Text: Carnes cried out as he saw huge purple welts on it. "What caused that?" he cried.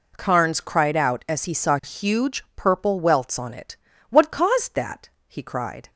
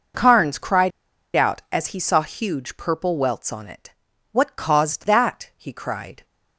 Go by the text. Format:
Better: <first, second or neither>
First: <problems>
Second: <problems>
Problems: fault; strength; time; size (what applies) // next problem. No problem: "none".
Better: first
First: none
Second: pauses between "cried" and "out"; noticeable; at 0.9 s; 0.46 s long